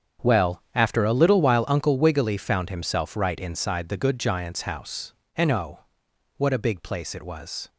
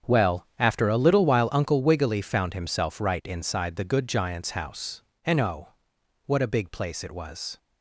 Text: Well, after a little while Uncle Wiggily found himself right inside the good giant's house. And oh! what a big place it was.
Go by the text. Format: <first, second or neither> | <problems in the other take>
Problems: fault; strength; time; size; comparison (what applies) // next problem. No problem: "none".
neither | starts louder than the rest; strong; the same in both